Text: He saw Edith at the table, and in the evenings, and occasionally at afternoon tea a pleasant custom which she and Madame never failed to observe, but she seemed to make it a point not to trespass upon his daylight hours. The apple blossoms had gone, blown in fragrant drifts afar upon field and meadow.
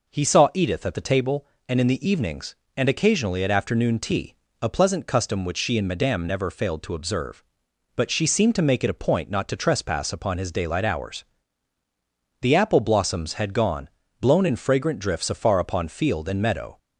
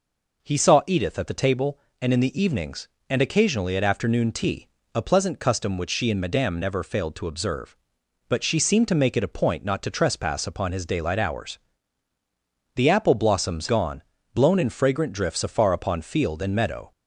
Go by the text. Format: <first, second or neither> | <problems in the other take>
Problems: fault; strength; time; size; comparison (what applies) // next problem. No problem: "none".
first | pauses between "tea" and "a"; slight; at 4.6 s; 0.26 s long; slight in the first // skips "had"; at 13.6 s